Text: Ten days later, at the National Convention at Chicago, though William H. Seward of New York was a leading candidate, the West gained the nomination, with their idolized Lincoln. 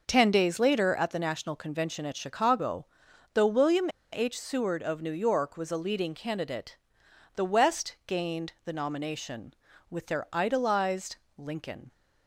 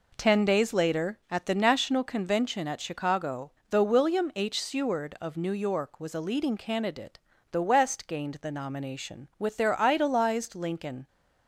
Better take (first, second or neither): second